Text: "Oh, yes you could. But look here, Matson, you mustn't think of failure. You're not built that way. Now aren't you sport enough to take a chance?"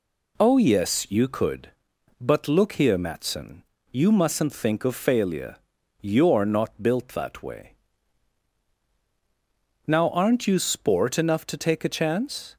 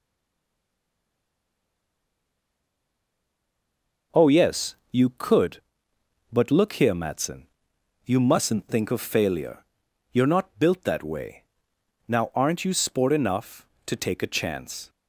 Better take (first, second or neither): first